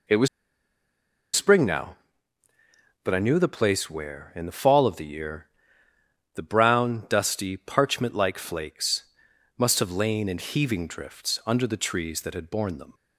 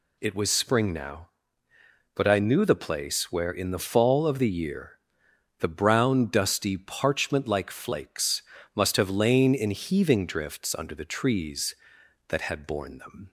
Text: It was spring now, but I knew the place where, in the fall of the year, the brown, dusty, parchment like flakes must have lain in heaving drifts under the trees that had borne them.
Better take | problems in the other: second | pauses between "was" and "spring"; at 0.2 s; 1.0 s long // pauses between "flakes" and "must"; noticeable; at 9.0 s; 0.54 s long; slight in the second

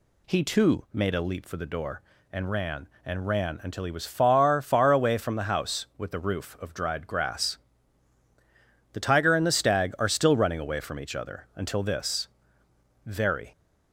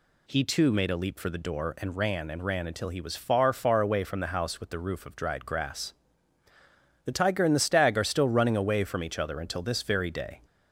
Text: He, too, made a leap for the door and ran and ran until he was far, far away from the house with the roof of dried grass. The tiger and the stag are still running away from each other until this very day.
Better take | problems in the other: second | pauses between "this" and "very"; noticeable; at 12.2 s; 0.78 s long // stops before "day"; at 13.5 s

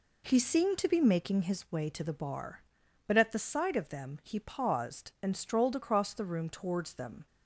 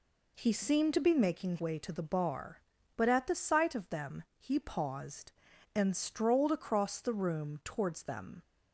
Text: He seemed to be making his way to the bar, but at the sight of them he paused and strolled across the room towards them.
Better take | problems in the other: first | skips "his"; at 1.5 s // pauses between "them" and "he"; slight; at 4.2 s; 0.16 s long

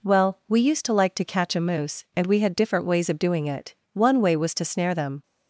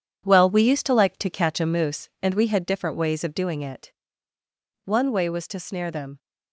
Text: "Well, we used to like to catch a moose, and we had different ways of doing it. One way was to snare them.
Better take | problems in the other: first | gets quieter; strong; throughout; 8 dB

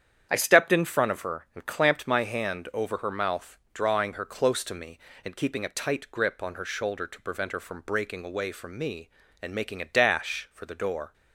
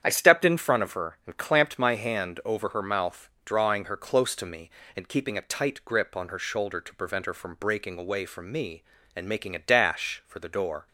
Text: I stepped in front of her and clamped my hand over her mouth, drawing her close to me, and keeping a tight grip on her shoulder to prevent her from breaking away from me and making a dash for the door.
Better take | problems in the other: neither | starts louder than the rest; strong; the same in both

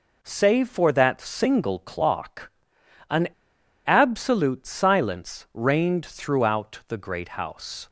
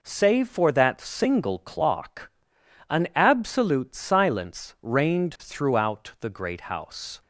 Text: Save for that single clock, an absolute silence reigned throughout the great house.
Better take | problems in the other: second | pauses between "an" and "absolute"; noticeable; at 3.2 s; 0.59 s long

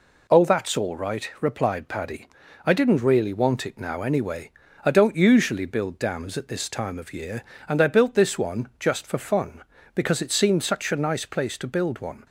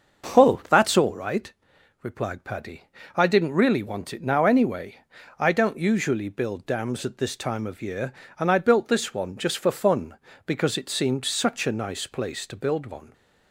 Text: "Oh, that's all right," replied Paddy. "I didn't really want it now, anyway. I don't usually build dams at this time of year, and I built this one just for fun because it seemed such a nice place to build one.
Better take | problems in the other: first | starts louder than the rest; noticeable; until 1.6 s; 6 dB

